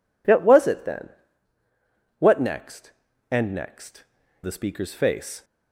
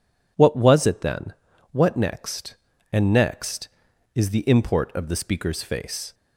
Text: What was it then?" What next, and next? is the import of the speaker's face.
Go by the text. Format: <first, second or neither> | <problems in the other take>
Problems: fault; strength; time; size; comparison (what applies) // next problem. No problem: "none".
second | skips "is the import of"; at 4.2 s